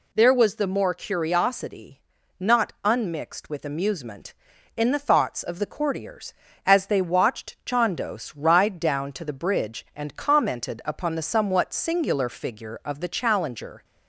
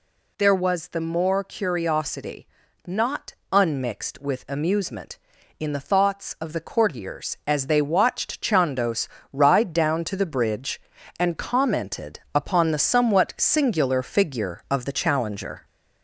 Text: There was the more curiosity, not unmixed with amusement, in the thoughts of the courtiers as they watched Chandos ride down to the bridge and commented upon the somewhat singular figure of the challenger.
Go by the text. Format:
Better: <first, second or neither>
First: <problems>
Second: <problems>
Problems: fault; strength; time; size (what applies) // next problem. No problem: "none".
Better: first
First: none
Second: gets louder; slight; throughout; 3 dB // pauses between "not" and "unmixed"; slight; at 3.3 s; 0.18 s long // pauses between "Chandos" and "ride"; slight; at 9.0 s; 0.24 s long // pauses between "commented" and "upon"; slight; at 12.1 s; 0.16 s long